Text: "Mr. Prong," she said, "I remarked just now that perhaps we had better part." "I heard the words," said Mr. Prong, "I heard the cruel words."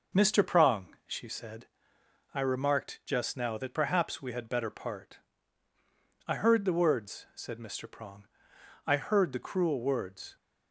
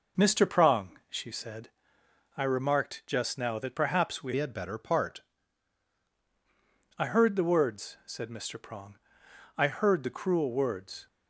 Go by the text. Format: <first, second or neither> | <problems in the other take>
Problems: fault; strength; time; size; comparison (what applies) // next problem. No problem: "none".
first | changes voice from "had" to "part"; from 4.3 to 5.2 s; 0.9 s long